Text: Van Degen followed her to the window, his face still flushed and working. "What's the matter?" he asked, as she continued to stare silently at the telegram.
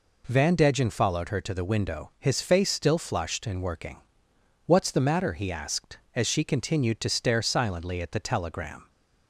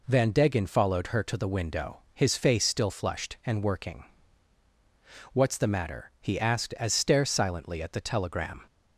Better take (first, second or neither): first